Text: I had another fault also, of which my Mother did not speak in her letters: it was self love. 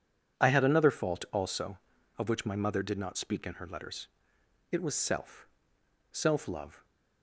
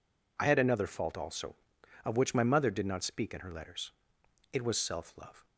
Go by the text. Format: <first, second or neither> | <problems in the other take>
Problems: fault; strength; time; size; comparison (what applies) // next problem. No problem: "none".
second | says "self" twice; at 6.1 s